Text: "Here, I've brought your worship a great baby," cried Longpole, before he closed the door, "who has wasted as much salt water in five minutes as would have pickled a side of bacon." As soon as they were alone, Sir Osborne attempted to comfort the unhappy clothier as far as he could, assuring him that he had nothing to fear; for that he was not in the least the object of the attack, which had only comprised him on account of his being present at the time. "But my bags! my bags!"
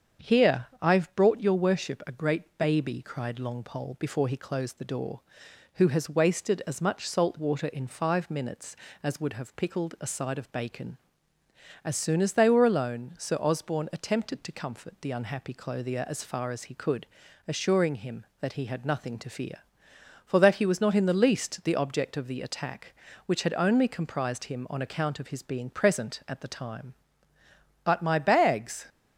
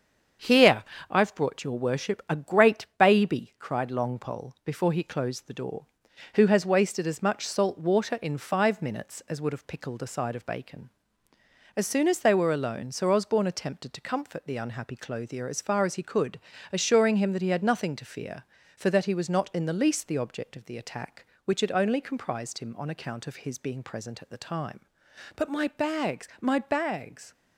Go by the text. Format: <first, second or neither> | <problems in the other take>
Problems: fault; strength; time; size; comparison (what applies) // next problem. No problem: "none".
second | starts louder than the rest; strong; until 1.4 s; 7.5 dB; also in the second // stops before "my bags"; at 28.8 s